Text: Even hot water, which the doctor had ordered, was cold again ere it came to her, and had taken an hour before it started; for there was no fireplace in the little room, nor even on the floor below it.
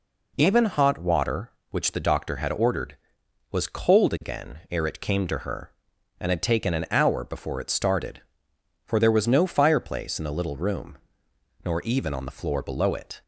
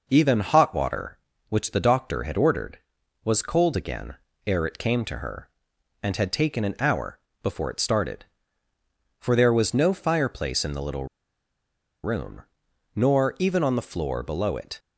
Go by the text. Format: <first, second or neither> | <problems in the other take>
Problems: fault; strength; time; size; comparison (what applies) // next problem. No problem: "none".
first | pauses between "again" and "ere"; slight; at 4.1 s; 0.30 s long // pauses between "hour" and "before"; slight; at 7.1 s; 0.24 s long // pauses between "little" and "room"; at 11.0 s; 0.98 s long